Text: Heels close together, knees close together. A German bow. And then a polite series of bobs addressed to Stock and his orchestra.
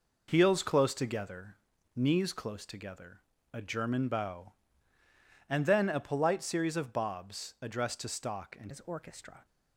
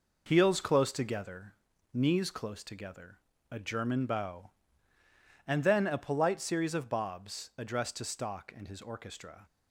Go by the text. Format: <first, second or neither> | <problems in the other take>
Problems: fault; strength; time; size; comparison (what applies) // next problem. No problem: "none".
second | changes voice at "his"; from 8.7 s on; 0.7 s long